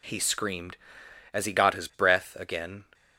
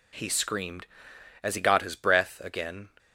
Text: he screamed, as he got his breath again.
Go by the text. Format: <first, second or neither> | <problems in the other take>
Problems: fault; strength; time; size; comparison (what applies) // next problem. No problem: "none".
neither | none